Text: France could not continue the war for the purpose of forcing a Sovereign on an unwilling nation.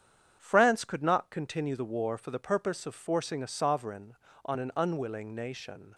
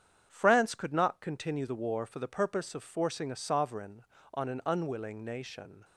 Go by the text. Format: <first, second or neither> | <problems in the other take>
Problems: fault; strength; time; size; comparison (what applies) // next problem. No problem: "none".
neither | starts louder than the rest; strong; the same in both